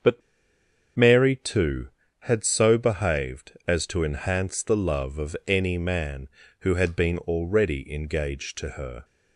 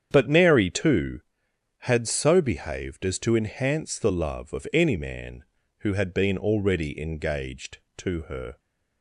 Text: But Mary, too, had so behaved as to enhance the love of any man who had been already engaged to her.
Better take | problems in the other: second | starts louder than the rest; until 1.7 s; 7 dB; strong in the second // pauses between "But" and "Mary"; noticeable; at 0.2 s; 0.75 s long

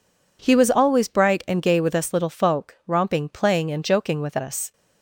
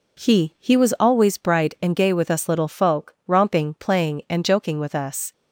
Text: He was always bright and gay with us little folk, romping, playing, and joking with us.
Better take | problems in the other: first | says "He" twice; at 0.5 s

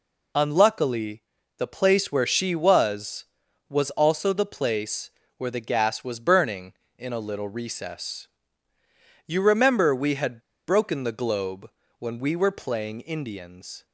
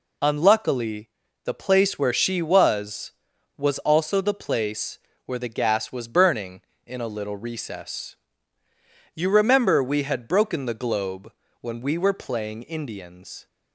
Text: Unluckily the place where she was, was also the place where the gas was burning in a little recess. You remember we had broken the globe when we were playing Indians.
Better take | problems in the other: second | pauses between "Unluckily" and "the"; slight; at 1.2 s; 0.34 s long; slight in the second // pauses between "place" and "where"; slight; at 5.1 s; 0.26 s long; slight in the second // pauses between "had" and "broken"; slight; at 10.4 s; 0.26 s long // pauses between "globe" and "when"; slight; at 11.6 s; 0.30 s long; slight in the second

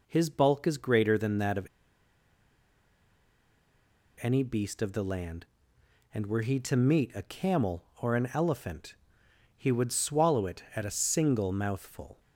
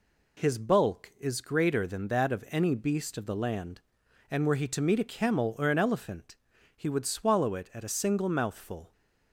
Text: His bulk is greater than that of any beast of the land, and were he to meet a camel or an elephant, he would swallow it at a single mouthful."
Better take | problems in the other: second | pauses between "of" and "any"; strong; at 1.6 s; 2.5 s long

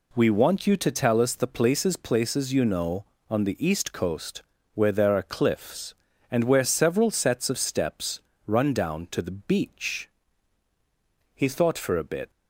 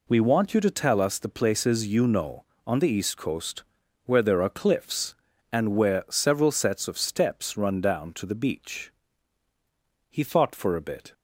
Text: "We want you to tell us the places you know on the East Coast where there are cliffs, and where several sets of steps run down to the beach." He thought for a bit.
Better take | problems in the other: second | says "places" twice; at 1.9 s // pauses between "Coast" and "where"; slight; at 4.4 s; 0.32 s long; also in the second // pauses between "steps" and "run"; slight; at 8.1 s; 0.26 s long

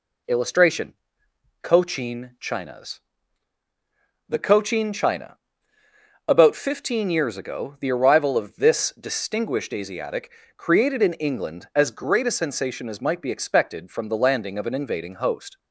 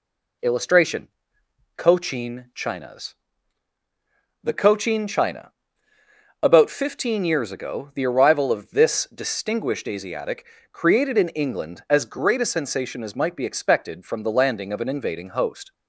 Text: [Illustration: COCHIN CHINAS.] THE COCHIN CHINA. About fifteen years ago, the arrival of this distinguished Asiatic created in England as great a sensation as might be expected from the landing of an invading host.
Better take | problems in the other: neither | pauses between "Asiatic" and "created"; slight; the same in both

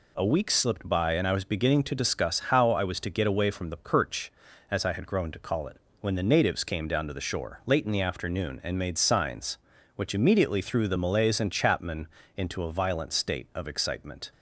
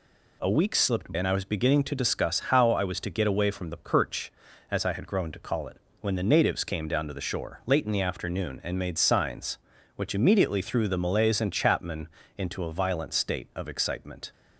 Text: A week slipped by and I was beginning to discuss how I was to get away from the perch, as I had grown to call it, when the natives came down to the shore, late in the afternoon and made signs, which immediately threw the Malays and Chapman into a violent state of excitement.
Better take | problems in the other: first | skips "by"; at 1.1 s // pauses between "Chapman" and "into"; slight; at 12.0 s; 0.30 s long; slight in the first

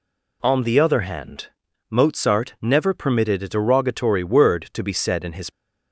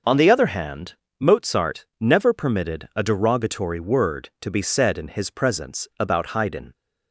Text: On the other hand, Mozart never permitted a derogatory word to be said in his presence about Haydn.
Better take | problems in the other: second | stops before "presence about Haydn"; at 5.4 s

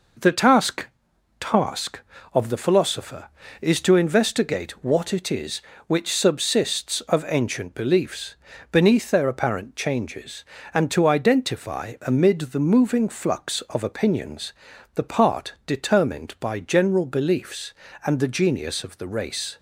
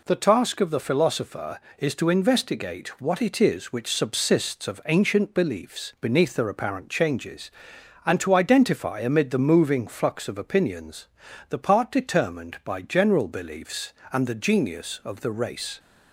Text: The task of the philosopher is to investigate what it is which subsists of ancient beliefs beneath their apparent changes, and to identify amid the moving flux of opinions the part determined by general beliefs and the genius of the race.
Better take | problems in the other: second | says "task" twice; at 1.3 s // pauses between "beliefs" and "beneath"; at 8.3 s; 0.38 s long // pauses between "opinions" and "the"; at 14.5 s; 0.42 s long; also in the second

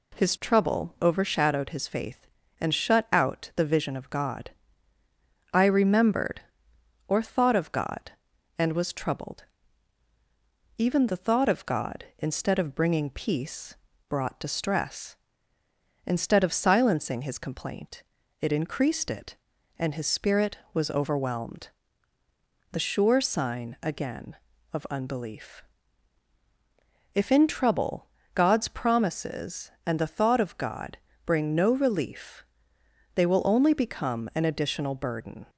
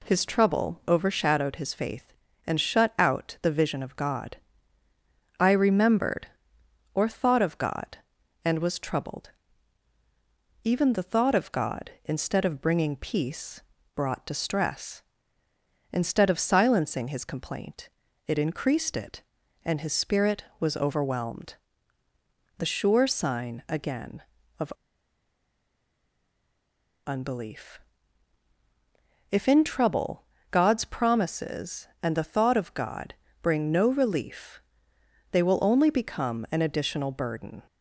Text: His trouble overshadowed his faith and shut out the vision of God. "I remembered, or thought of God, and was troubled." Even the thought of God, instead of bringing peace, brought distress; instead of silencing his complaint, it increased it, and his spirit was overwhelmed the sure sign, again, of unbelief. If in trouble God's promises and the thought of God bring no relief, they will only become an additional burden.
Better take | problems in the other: first | pauses between "overwhelmed" and "the"; at 21.5 s; 1.0 s long; also in the first // pauses between "of" and "unbelief"; strong; at 24.7 s; 2.3 s long // pauses between "trouble" and "God's"; slight; at 30.2 s; 0.24 s long; slight in the first // pauses between "God" and "bring"; slight; at 33.1 s; 0.26 s long; slight in the first

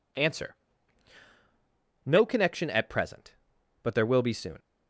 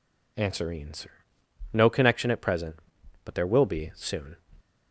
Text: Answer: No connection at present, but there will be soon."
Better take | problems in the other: first | says "Answer" twice; at 0.7 s

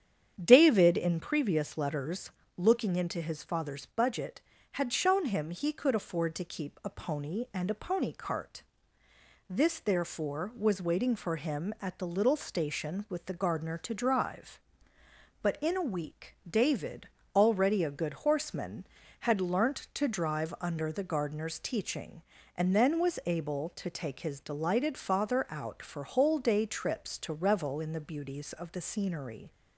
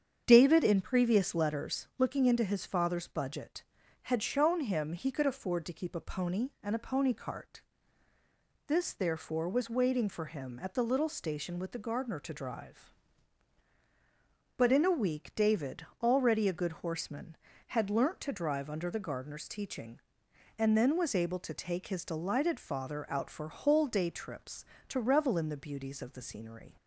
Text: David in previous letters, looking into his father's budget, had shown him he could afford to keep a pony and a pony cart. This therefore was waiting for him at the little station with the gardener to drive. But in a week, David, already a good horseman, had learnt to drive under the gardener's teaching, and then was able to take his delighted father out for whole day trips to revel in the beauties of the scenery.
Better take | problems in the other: neither | starts louder than the rest; strong; the same in both

